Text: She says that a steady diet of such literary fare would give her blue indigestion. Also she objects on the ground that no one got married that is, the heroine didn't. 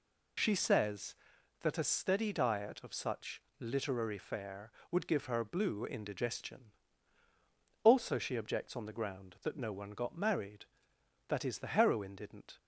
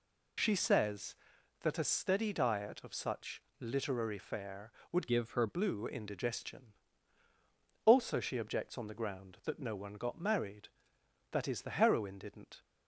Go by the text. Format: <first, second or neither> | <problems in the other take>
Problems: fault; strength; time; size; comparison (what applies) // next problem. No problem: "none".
first | pauses between "such" and "literary"; slight; at 3.4 s; 0.18 s long; slight in the first // changes voice from "give" to "her"; from 5.0 to 5.4 s; 0.4 s long